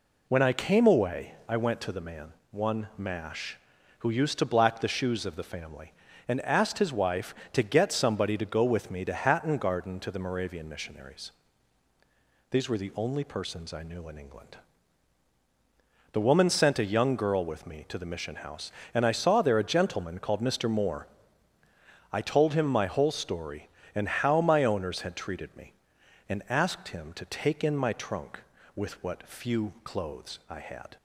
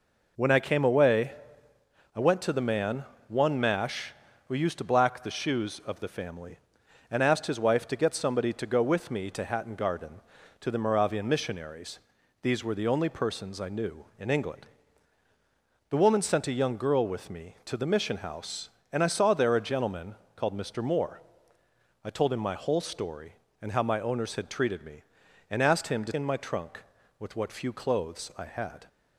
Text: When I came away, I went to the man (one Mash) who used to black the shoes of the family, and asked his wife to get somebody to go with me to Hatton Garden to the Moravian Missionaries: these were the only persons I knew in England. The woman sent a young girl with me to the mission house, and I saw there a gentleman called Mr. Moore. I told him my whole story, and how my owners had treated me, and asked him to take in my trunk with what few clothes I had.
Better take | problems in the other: first | pauses between "gentleman" and "called"; slight; at 20.1 s; 0.18 s long // skips "take"; at 26.1 s

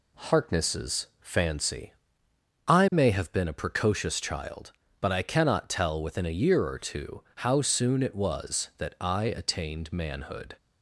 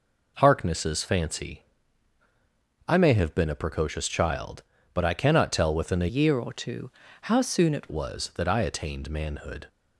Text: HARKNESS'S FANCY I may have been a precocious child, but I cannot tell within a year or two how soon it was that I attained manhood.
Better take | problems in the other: first | pauses between "FANCY" and "I"; strong; at 1.6 s; 1.2 s long; noticeable in the first // changes voice from "year" to "it"; from 6.1 to 7.8 s; 1.7 s long // pauses between "two" and "how"; slight; at 6.9 s; 0.32 s long

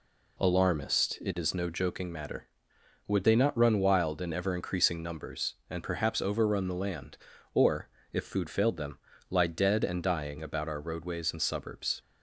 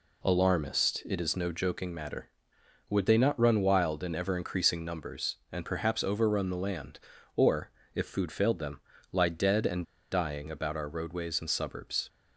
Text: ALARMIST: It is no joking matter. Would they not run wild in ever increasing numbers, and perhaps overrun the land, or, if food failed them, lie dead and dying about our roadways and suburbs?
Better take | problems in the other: first | pauses between "and" and "dying"; slight; at 9.8 s; 0.27 s long

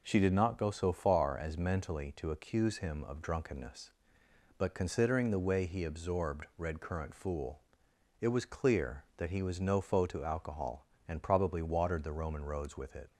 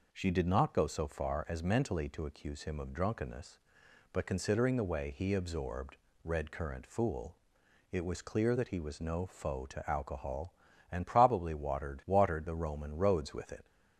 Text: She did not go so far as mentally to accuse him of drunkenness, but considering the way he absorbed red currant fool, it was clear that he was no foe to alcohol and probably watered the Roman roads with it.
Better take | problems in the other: first | pauses between "absorbed" and "red"; slight; at 5.9 s; 0.28 s long // says "watered" twice; at 12.0 s

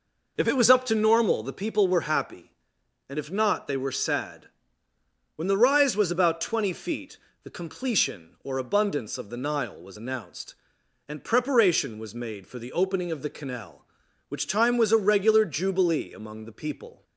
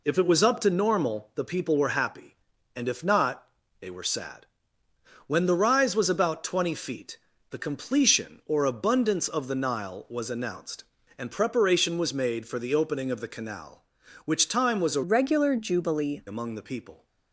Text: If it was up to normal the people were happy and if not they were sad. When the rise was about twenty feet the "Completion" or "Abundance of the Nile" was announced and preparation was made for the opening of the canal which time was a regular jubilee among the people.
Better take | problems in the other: first | pauses between "not" and "they"; slight; at 3.4 s; 0.36 s long // pauses between "feet" and "the"; slight; at 7.1 s; 0.34 s long; slight in the first // changes voice from "regular" to "jubilee"; from 15.0 to 16.2 s; 1.2 s long

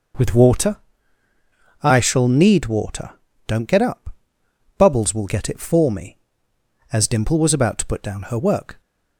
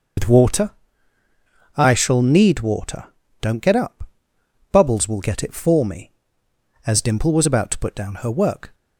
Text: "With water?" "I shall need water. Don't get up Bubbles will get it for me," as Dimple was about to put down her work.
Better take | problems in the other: first | loses the start of "With"; at 0.1 s; 85 ms // pauses between "up" and "Bubbles"; noticeable; at 4.0 s; 0.64 s long; noticeable in the first

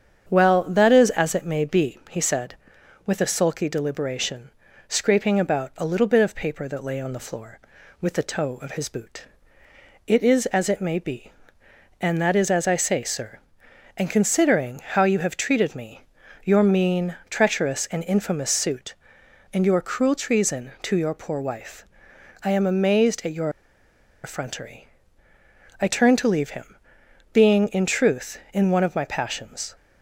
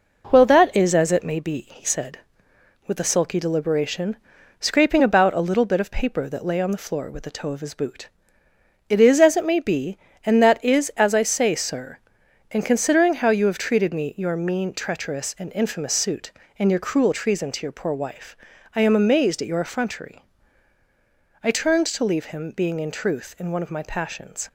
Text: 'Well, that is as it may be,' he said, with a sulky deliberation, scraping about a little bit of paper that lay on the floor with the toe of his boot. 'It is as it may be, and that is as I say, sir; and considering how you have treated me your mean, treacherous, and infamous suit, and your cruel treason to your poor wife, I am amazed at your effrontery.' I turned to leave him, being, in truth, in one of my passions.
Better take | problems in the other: second | starts louder than the rest; strong; until 1.3 s; 8 dB // pauses between "me" and "your"; at 16.0 s; 0.42 s long // pauses between "your" and "effrontery"; noticeable; at 23.4 s; 0.74 s long

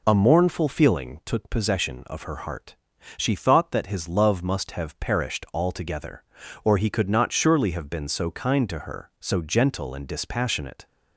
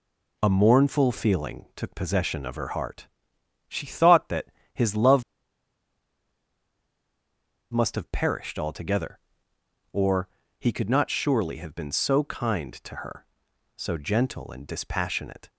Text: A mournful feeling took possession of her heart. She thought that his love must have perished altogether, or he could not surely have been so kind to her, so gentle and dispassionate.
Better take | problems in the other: first | pauses between "that" and "his"; slight; at 4.4 s; 0.26 s long // pauses between "love" and "must"; strong; at 5.2 s; 2.5 s long // pauses between "or" and "he"; slight; at 10.2 s; 0.32 s long

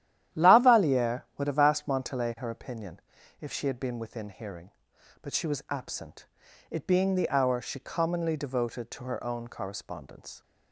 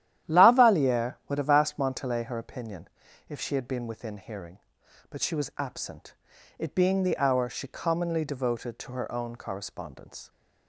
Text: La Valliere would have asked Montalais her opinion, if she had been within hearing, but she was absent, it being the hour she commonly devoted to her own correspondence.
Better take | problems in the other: neither | starts louder than the rest; strong; the same in both

